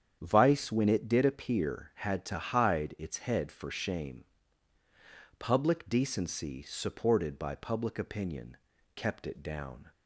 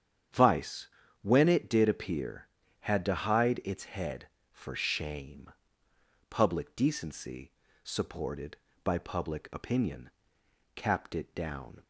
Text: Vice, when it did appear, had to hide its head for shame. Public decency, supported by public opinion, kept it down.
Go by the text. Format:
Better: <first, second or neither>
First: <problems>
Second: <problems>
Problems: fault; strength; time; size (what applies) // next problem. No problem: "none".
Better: first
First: starts louder than the rest; strong; until 1.2 s; 8.5 dB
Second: starts louder than the rest; strong; until 1.6 s; 8.5 dB // says "capped" for "kept"; at 10.7 s